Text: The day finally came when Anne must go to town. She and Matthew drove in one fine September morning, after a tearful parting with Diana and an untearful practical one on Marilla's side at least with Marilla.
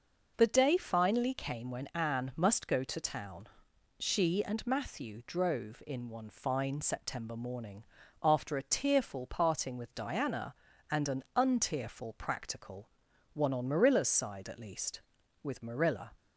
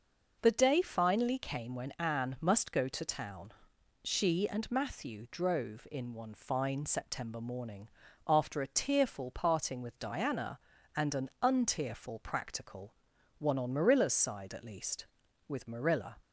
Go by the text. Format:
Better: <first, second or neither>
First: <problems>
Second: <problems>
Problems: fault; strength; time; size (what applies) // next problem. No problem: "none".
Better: neither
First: pauses between "practical" and "one"; noticeable; at 12.8 s; 0.46 s long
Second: pauses between "practical" and "one"; noticeable; at 12.9 s; 0.46 s long